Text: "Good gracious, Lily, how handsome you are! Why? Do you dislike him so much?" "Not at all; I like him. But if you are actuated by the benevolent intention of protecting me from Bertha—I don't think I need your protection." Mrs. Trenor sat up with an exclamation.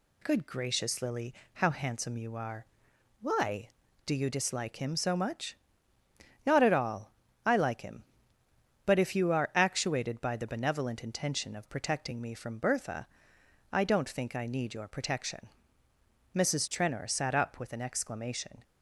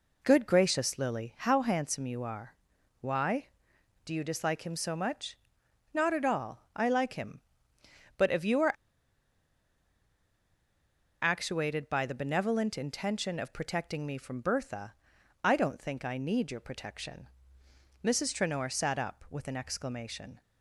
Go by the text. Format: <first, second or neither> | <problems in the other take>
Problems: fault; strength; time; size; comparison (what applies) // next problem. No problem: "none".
first | pauses between "are" and "actuated"; strong; at 8.7 s; 2.5 s long